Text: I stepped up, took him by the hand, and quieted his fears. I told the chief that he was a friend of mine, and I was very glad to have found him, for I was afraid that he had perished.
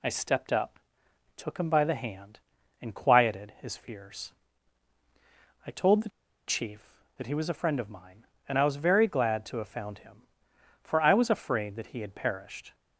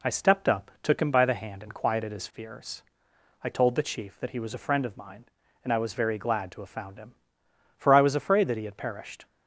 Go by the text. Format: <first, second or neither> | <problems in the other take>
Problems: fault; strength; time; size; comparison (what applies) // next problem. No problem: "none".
second | pauses between "the" and "chief"; at 6.0 s; 0.38 s long